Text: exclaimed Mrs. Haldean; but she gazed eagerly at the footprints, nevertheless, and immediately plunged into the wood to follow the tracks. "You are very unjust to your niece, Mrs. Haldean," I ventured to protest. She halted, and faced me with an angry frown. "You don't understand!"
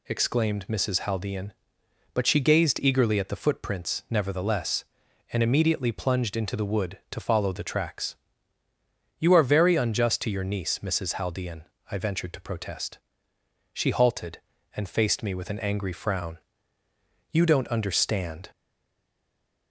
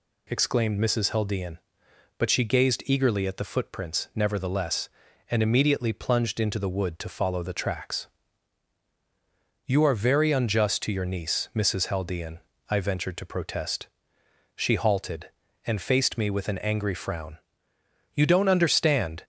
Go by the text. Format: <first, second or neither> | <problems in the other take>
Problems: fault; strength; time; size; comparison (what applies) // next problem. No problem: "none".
second | stays silent after the last word; noticeable; from 18.5 s on; 1.2 s long